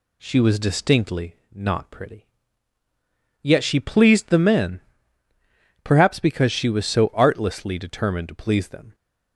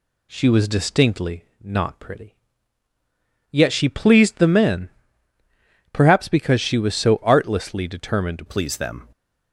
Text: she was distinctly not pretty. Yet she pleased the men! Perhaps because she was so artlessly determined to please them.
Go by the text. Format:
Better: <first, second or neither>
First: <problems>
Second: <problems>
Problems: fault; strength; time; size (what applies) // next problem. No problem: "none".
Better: first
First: pauses between "distinctly" and "not"; slight; at 1.3 s; 0.18 s long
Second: pauses between "distinctly" and "not"; slight; at 1.4 s; 0.18 s long // changes voice at "please"; from 8.4 s on; 0.6 s long